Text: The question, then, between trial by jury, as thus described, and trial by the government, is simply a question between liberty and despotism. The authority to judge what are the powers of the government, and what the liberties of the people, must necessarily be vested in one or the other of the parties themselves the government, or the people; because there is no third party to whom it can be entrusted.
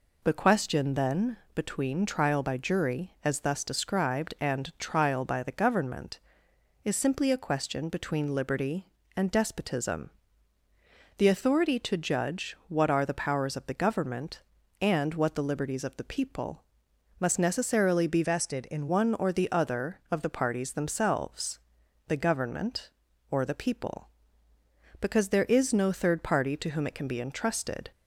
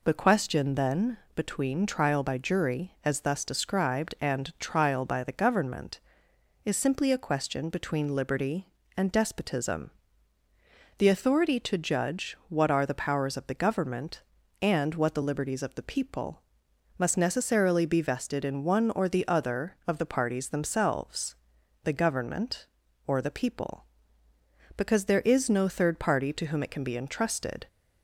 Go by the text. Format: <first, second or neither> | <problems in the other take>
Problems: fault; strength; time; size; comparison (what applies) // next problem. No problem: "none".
second | changes voice from "vested" to "in"; from 18.2 to 18.8 s; 0.6 s long // pauses between "themselves" and "the"; noticeable; at 21.5 s; 0.48 s long; noticeable in the second